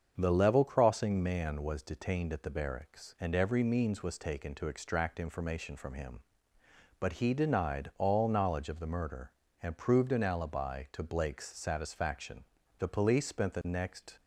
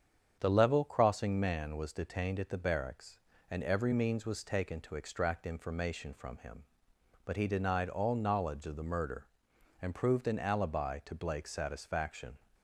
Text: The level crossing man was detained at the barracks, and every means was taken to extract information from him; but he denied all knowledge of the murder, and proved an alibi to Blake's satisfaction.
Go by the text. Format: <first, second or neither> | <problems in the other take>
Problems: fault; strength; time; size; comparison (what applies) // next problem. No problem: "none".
second | starts louder than the rest; until 1.1 s; 7 dB; strong in the second // goes on to say "The police spent the next"; from 12.7 s on; 1.4 s long